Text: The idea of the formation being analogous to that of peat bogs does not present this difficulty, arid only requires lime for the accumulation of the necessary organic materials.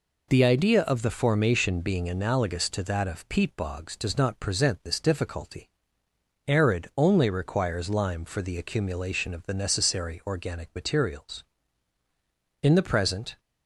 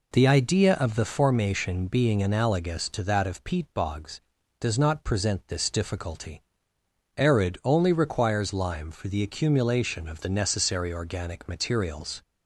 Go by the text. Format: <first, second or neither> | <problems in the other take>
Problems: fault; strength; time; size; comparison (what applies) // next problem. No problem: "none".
second | goes on to say "In the present"; noticeable; from 12.6 s on; 0.78 s long